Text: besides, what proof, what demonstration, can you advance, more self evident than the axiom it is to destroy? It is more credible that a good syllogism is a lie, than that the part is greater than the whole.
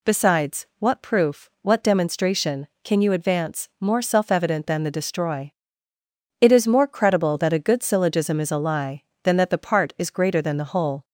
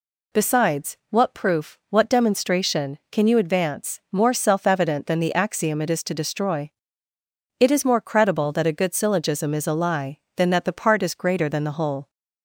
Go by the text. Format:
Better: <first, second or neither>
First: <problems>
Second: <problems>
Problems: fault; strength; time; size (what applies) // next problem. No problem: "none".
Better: second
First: skips "axiom it is to"; at 4.9 s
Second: none